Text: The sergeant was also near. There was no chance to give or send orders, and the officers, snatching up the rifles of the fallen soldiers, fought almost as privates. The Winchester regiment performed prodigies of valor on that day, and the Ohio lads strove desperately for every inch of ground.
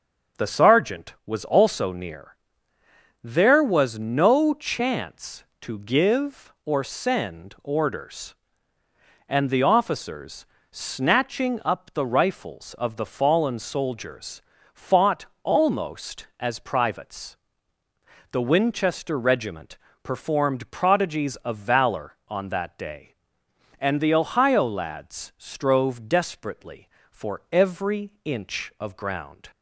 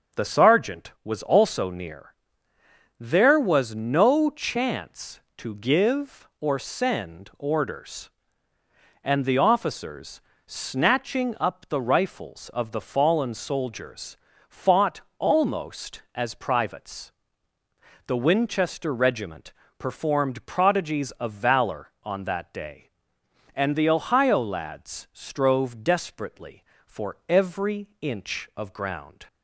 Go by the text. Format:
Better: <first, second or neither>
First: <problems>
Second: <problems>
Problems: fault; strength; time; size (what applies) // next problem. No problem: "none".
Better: neither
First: starts louder than the rest; until 1.4 s; 6.5 dB // pauses between "fought" and "almost"; slight; at 15.2 s; 0.20 s long // pauses between "regiment" and "performed"; slight; at 19.7 s; 0.26 s long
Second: starts louder than the rest; until 1.2 s; 6.5 dB // pauses between "fought" and "almost"; slight; at 15.0 s; 0.20 s long // pauses between "regiment" and "performed"; slight; at 19.5 s; 0.26 s long